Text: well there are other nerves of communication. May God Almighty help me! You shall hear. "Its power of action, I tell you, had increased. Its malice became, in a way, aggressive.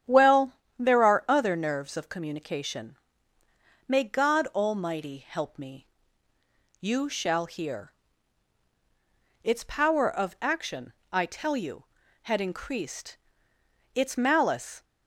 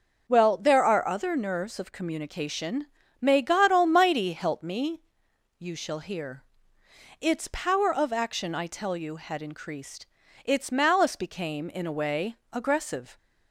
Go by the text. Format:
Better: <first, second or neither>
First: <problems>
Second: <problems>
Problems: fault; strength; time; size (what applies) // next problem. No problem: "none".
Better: second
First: starts louder than the rest; strong; until 1.3 s; 9.5 dB // pauses between "well" and "there"; slight; at 0.5 s; 0.26 s long // stops before "became in a way aggressive"; at 14.8 s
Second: none